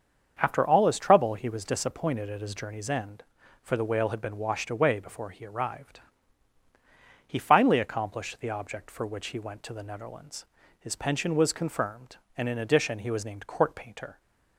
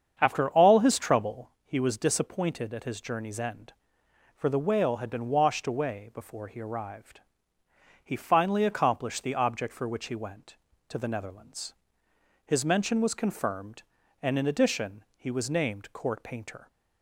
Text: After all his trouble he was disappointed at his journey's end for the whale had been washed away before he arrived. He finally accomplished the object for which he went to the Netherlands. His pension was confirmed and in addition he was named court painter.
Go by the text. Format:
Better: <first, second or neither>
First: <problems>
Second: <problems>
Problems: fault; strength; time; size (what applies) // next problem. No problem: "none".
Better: first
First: starts louder than the rest; until 1.4 s; 7 dB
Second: starts louder than the rest; strong; until 1.1 s; 7.5 dB // says "mention" for "pension"; at 12.6 s